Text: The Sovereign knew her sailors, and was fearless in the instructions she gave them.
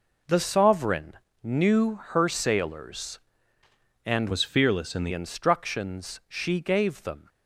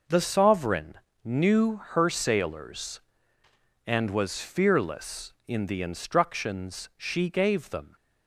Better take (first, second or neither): second